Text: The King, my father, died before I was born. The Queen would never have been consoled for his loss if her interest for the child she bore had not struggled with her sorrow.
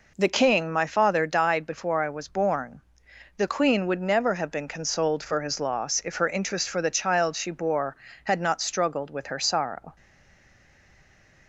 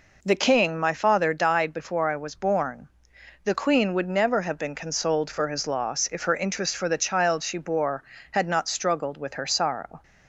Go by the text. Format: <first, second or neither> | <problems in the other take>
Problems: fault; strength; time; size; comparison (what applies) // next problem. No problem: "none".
second | stays silent after the last word; noticeable; from 9.9 s on; 1.5 s long